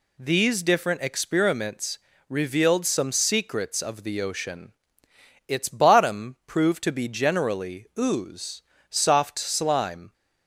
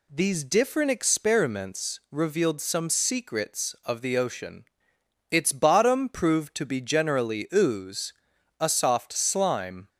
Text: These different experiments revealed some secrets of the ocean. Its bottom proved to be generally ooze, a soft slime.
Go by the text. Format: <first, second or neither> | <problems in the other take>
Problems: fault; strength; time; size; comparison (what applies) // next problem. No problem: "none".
second | pauses between "experiments" and "revealed"; slight; at 1.9 s; 0.32 s long // skips "a"; at 8.7 s